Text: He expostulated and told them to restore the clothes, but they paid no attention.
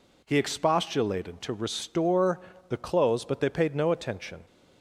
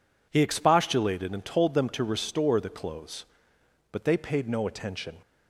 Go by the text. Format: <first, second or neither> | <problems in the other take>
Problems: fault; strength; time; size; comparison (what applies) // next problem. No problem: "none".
second | skips "and told them"; at 1.4 s // pauses between "restore" and "the"; slight; at 2.4 s; 0.28 s long